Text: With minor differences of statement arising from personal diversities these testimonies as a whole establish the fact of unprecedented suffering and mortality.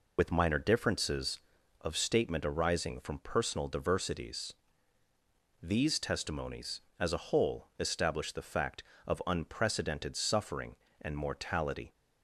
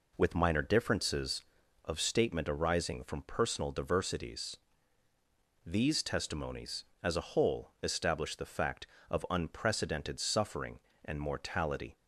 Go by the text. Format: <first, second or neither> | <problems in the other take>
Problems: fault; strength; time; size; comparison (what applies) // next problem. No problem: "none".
second | loses the start of "With"; at 0.1 s; 80 ms // pauses between "diversities" and "these"; at 4.5 s; 1.1 s long; also in the second